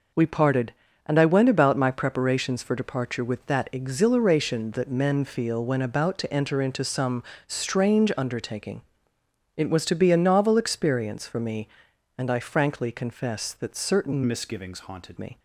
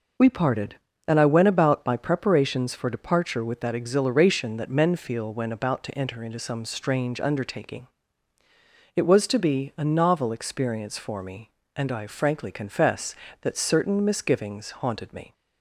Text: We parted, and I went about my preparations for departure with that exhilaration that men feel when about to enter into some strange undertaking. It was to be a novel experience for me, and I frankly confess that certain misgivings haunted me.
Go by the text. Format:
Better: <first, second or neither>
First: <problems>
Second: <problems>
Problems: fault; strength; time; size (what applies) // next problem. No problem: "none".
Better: second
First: pauses between "some" and "strange"; slight; at 7.2 s; 0.24 s long // changes voice from "misgivings" to "haunted"; from 14.2 to 15.1 s; 0.9 s long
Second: none